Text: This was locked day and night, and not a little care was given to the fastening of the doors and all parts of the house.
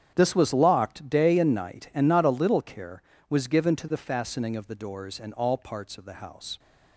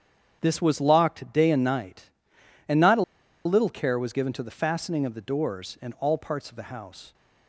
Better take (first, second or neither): first